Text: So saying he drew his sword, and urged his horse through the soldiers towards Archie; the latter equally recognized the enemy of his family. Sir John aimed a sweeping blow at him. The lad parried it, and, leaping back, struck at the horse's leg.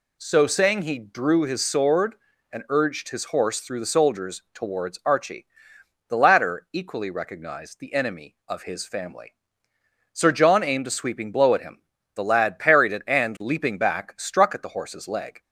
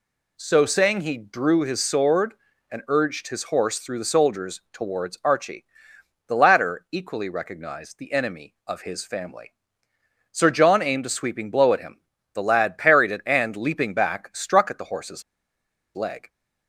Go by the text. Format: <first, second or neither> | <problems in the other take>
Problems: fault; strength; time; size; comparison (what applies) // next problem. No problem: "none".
first | pauses between "horse's" and "leg"; noticeable; at 15.2 s; 0.72 s long